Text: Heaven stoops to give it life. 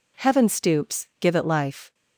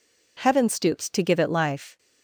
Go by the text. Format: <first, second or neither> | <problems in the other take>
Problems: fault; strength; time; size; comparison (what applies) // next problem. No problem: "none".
second | skips "to"; at 1.1 s